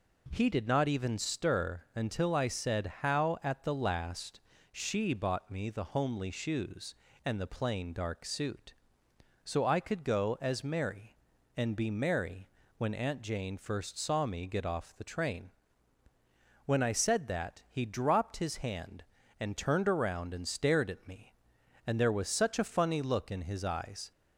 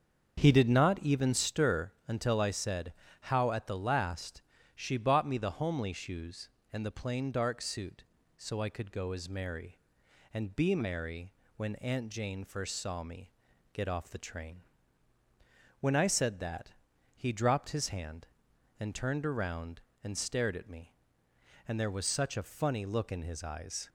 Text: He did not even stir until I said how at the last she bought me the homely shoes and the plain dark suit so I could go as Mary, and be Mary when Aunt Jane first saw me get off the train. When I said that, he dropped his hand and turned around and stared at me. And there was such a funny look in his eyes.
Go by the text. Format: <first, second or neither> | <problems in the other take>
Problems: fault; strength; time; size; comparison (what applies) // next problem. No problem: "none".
first | starts louder than the rest; until 1.6 s; 7 dB // pauses between "stir" and "until"; slight; at 1.9 s; 0.16 s long // pauses between "said" and "how"; slight; at 2.9 s; 0.30 s long // pauses between "last" and "she"; slight; at 4.4 s; 0.36 s long; slight in the first // pauses between "Mary" and "when"; slight; at 11.3 s; 0.24 s long; slight in the first // pauses between "me" and "get"; at 13.3 s; 0.42 s long